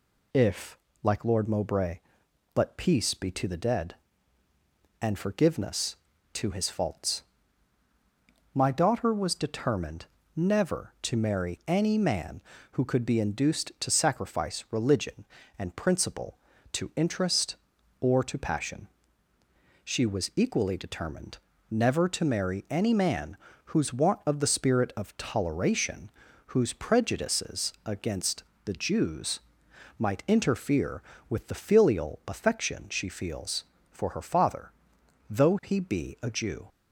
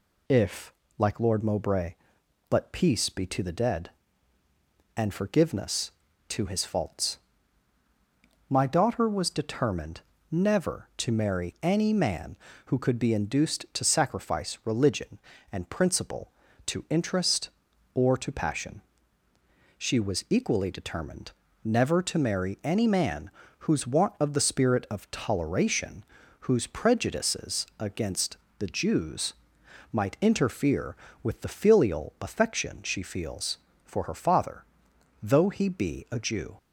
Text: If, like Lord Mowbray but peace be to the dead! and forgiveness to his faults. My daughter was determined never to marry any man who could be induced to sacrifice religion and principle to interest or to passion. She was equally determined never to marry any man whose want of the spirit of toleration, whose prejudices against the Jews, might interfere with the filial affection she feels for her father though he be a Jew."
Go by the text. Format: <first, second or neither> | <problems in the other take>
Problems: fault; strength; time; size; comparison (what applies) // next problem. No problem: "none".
neither | pauses between "determined" and "never"; slight; the same in both // pauses between "determined" and "never"; slight; the same in both // pauses between "man" and "whose"; slight; the same in both // pauses between "against" and "the"; slight; the same in both // pauses between "father" and "though"; noticeable; the same in both